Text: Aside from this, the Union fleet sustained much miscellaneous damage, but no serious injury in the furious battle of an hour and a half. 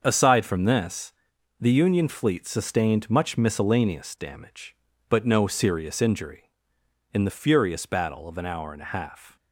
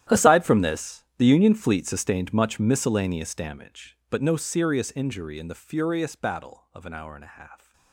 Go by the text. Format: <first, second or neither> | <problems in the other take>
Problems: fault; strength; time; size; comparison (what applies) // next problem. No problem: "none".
first | gets quieter; strong; throughout; 19 dB // starts louder than the rest; strong; until 1.2 s; 11.5 dB; also in the first